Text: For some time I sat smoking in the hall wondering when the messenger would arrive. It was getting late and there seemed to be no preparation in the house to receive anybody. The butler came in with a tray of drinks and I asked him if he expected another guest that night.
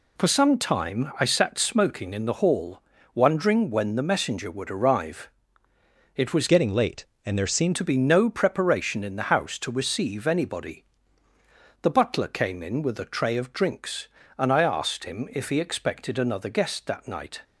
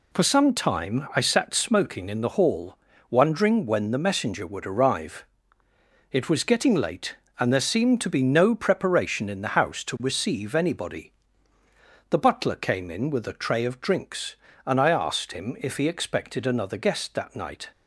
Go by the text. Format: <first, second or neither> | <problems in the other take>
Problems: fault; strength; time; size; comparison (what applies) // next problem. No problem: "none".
second | pauses between "hall" and "wondering"; slight; at 2.8 s; 0.32 s long; slight in the second // changes voice from "getting" to "seemed"; from 6.4 to 7.7 s; 1.3 s long